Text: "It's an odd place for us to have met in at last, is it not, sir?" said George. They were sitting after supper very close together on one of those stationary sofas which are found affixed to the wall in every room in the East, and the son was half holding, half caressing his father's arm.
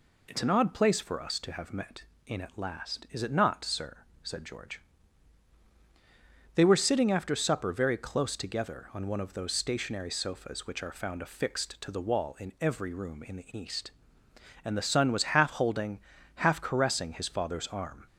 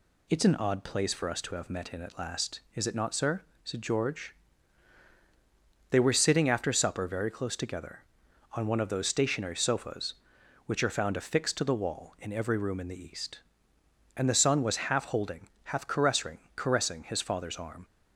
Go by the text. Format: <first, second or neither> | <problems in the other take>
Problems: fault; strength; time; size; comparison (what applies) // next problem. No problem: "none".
first | says "caressing" twice; at 16.5 s